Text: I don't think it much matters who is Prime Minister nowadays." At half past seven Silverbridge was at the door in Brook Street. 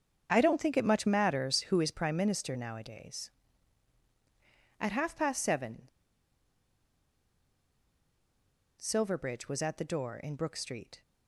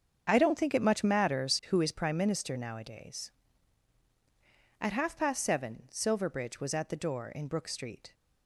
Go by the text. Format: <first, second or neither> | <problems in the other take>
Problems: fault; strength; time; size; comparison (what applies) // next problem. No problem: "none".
second | starts louder than the rest; until 1.3 s; 7 dB; also in the second // pauses between "seven" and "Silverbridge"; strong; at 5.8 s; 2.9 s long